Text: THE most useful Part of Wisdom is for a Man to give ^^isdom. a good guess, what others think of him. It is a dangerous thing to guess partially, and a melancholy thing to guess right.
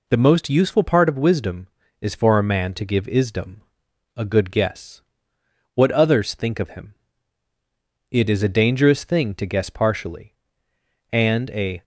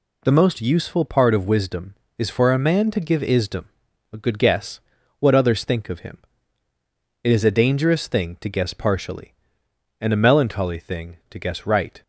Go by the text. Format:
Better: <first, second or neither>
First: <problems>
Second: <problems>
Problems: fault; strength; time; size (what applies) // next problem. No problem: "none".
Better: second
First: stops before "melancholy thing to guess right"; at 11.8 s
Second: none